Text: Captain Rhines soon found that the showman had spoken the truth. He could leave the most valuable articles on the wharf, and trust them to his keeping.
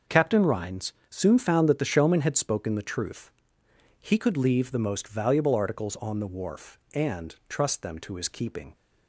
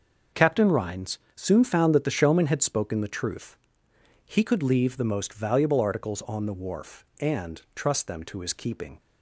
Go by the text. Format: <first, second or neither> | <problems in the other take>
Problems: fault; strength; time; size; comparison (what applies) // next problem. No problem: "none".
neither | starts louder than the rest; noticeable; the same in both // pauses between "Rhines" and "soon"; slight; the same in both